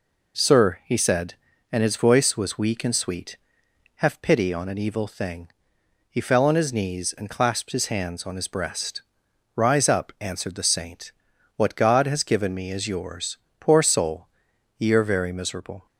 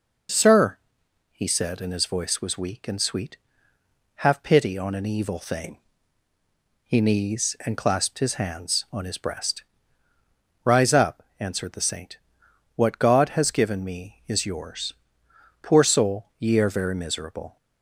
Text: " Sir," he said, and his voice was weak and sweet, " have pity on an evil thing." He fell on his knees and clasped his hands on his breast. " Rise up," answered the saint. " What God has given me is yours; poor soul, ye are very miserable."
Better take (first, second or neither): first